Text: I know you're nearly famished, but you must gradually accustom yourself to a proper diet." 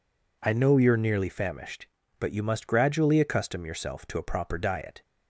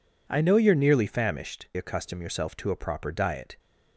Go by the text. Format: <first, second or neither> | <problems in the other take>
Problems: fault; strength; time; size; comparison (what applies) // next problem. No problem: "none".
first | skips "but you must gradually"; at 1.7 s